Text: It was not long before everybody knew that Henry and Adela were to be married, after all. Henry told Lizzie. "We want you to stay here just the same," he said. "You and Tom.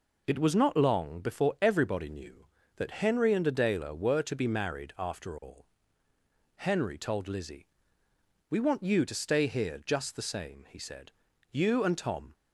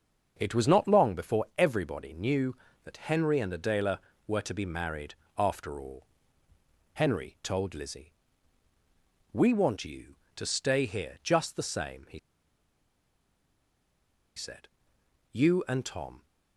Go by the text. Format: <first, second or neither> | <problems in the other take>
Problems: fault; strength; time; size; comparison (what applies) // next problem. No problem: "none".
first | starts louder than the rest; until 1.4 s; 6.5 dB // pauses between "he" and "said"; strong; at 12.1 s; 2.1 s long